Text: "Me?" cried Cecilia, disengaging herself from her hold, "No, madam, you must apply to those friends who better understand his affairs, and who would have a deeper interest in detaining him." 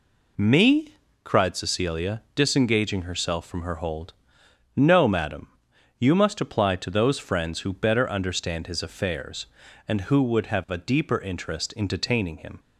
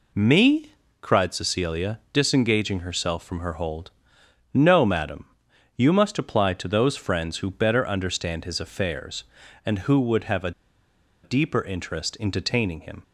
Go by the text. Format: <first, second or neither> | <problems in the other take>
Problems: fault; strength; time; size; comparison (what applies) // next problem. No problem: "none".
first | pauses between "a" and "deeper"; noticeable; at 10.5 s; 0.72 s long